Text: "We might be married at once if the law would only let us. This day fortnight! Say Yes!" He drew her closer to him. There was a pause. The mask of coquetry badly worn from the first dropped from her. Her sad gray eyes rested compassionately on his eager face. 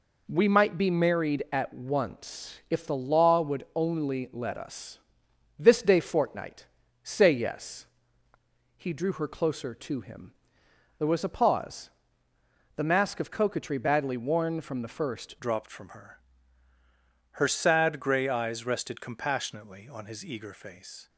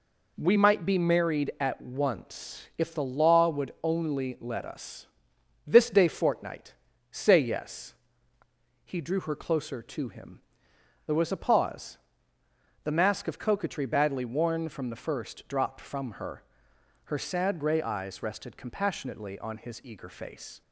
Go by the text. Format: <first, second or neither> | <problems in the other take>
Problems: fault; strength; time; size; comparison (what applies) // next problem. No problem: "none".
second | changes voice at "dropped"; from 15.3 s on; 5.7 s long